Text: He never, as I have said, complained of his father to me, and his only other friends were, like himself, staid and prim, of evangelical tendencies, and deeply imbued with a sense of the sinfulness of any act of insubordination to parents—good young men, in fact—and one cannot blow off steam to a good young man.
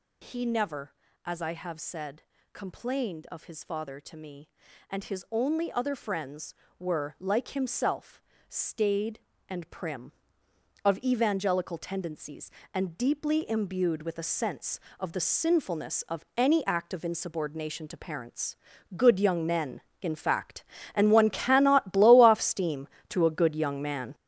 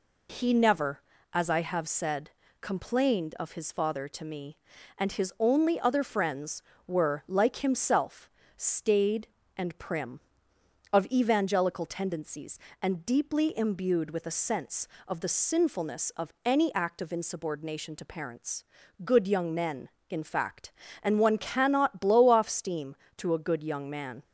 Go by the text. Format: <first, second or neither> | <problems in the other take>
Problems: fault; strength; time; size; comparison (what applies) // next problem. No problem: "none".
second | gets louder; strong; throughout; 8.5 dB